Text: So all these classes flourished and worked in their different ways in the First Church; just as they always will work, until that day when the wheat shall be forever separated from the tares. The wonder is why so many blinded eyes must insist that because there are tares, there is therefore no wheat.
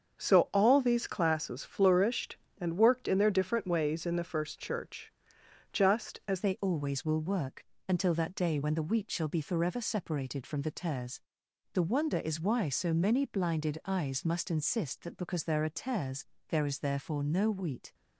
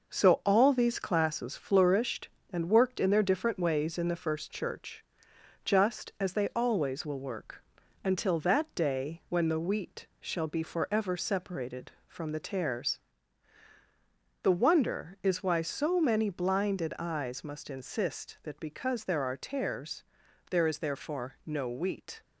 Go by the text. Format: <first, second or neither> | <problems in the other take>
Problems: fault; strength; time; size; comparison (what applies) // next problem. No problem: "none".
second | starts louder than the rest; until 1.2 s; 7 dB // changes voice at "they"; from 6.4 s on; 11.5 s long